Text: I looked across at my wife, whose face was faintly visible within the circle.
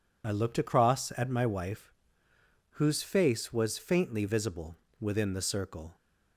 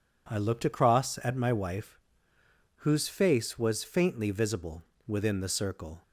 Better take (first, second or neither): second